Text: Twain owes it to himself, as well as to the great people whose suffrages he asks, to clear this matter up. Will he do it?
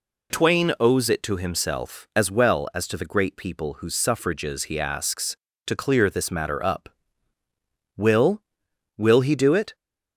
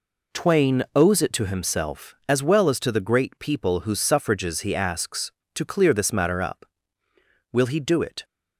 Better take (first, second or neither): second